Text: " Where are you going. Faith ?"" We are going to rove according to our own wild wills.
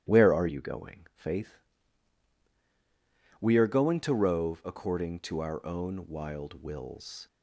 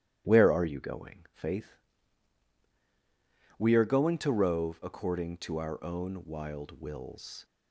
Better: neither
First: starts louder than the rest; strong; until 1.2 s; 8.5 dB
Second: starts louder than the rest; strong; until 1.3 s; 8.5 dB

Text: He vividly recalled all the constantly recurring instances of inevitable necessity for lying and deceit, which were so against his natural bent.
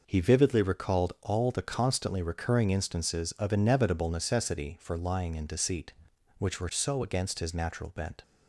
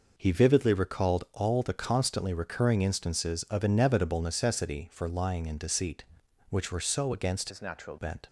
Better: first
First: none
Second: changes voice from "his" to "natural"; from 7.4 to 7.9 s; 0.5 s long

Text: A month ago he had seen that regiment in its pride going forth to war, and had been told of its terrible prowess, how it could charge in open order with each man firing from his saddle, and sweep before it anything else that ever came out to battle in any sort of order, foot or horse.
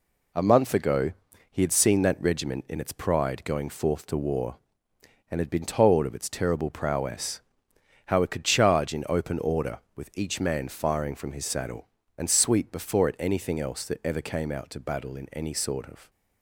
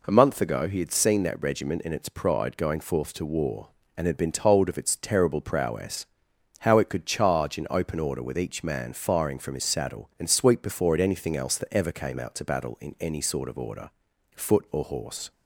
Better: second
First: pauses between "ago" and "he"; at 1.1 s; 0.38 s long // stops before "order foot or horse"; at 16.0 s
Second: none

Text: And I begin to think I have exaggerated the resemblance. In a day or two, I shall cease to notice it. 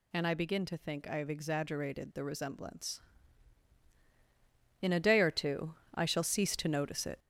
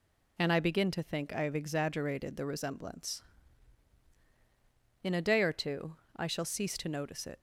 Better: second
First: gets louder; noticeable; throughout; 6 dB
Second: none

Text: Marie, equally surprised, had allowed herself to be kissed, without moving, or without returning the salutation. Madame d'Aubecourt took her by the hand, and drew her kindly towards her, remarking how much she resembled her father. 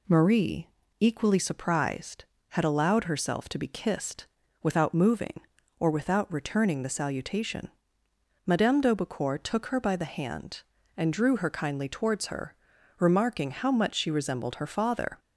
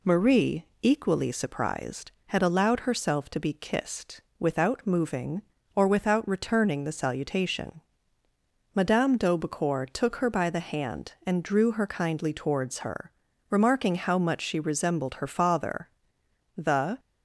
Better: first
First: none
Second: goes on to say "The"; slight; from 16.5 s on; 0.44 s long

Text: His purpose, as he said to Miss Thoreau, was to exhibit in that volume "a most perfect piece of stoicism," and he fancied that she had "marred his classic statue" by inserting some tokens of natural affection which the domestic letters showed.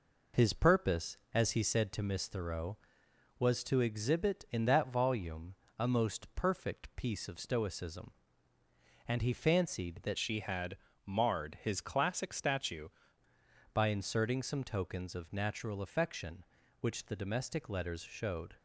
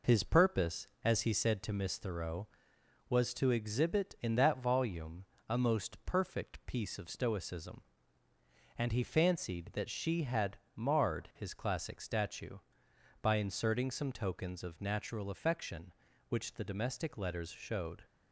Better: second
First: pauses between "volume" and "a"; slight; at 5.5 s; 0.24 s long // changes voice from "she" to "statue"; from 10.1 to 12.8 s; 2.7 s long // pauses between "had" and "marred"; slight; at 10.7 s; 0.30 s long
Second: pauses between "volume" and "a"; slight; at 5.2 s; 0.24 s long // pauses between "had" and "marred"; slight; at 10.5 s; 0.16 s long

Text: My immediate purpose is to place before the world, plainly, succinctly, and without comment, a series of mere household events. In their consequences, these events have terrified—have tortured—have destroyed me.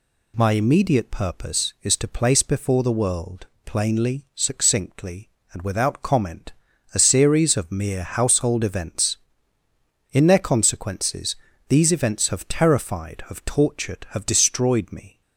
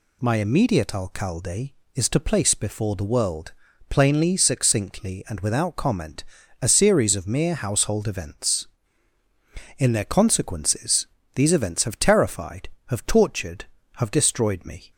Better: first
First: none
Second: says "alcalde" for "purpose"; at 0.9 s

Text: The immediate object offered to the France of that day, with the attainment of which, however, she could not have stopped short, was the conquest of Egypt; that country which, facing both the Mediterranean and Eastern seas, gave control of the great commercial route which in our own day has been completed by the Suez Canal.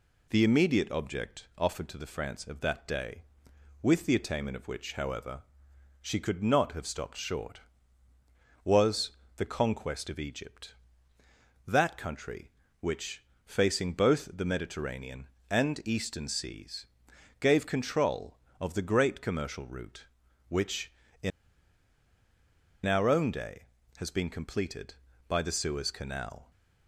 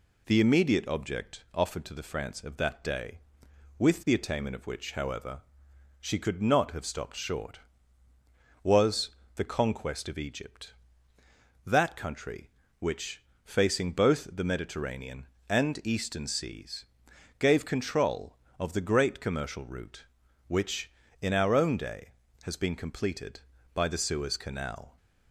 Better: second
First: pauses between "was" and "the"; slight; at 9.1 s; 0.26 s long // pauses between "in" and "our"; strong; at 21.3 s; 1.5 s long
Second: pauses between "was" and "the"; slight; at 9.1 s; 0.26 s long

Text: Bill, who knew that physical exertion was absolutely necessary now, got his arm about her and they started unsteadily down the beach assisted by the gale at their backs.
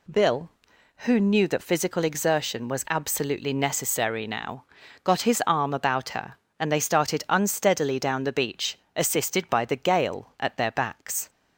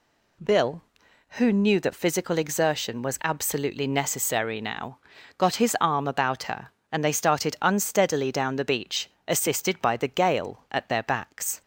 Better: neither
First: pauses between "beach" and "assisted"; slight; at 8.7 s; 0.18 s long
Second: pauses between "beach" and "assisted"; slight; at 9.0 s; 0.18 s long

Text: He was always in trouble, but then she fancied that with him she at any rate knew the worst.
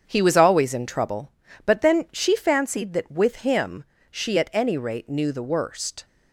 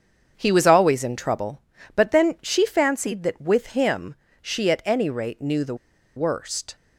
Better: first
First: starts louder than the rest; strong; until 1.0 s; 7 dB // pauses between "him" and "she"; slight; at 3.8 s; 0.26 s long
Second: starts louder than the rest; until 1.3 s; 7 dB // pauses between "him" and "she"; slight; at 4.1 s; 0.26 s long // pauses between "the" and "worst"; at 5.7 s; 0.41 s long

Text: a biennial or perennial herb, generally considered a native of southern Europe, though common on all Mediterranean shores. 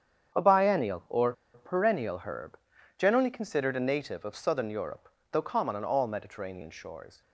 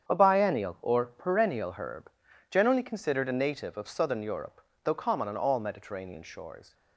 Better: second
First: starts louder than the rest; strong; until 1.6 s; 8 dB // pauses between "or" and "perennial"; slight; at 1.3 s; 0.21 s long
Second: starts louder than the rest; strong; until 1.1 s; 8 dB

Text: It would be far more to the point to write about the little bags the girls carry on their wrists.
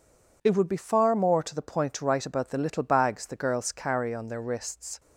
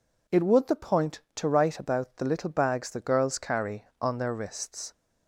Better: first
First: none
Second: skips "be far more to"; at 0.6 s

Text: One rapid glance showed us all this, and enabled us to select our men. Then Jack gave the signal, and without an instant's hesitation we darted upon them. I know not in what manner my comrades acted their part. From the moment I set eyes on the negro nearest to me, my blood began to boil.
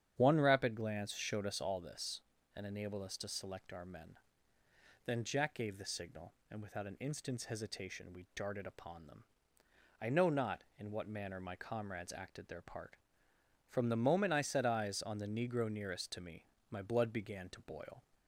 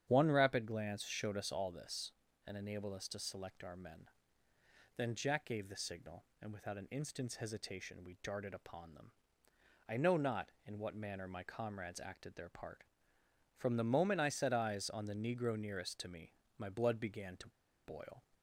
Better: first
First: starts louder than the rest; strong; until 1.1 s; 9 dB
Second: starts louder than the rest; strong; until 1.0 s; 9 dB // pauses between "to" and "boil"; slight; at 17.4 s; 0.35 s long

